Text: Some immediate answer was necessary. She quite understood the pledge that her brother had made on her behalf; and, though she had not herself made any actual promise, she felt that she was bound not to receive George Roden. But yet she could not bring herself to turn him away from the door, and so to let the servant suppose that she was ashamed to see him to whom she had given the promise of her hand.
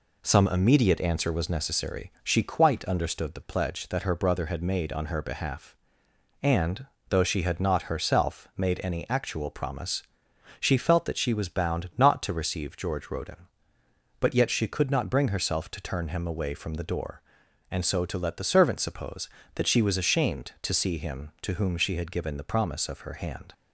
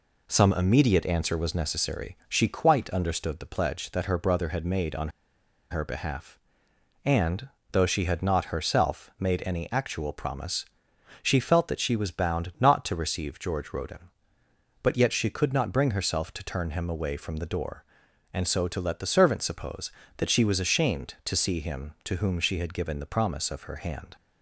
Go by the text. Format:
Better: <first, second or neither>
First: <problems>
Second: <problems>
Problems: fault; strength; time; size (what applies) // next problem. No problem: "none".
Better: first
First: none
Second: pauses between "on" and "her"; noticeable; at 5.0 s; 0.60 s long